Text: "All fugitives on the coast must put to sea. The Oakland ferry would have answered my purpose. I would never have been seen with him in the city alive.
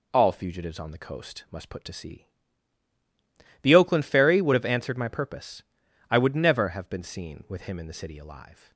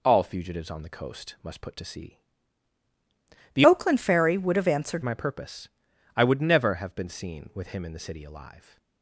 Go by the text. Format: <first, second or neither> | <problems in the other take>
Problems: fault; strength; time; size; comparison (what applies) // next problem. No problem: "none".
first | changes voice from "Oakland" to "answered"; from 3.6 to 5.0 s; 1.4 s long